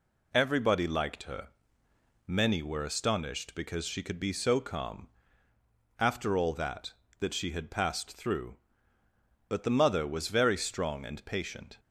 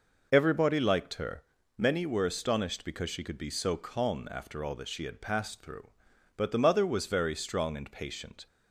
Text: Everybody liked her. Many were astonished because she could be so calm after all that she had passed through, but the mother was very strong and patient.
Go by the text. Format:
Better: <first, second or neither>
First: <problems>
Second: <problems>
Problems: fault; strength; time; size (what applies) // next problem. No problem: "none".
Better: second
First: pauses between "calm" and "after"; noticeable; at 5.0 s; 0.90 s long // says "that" twice; at 7.1 s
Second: none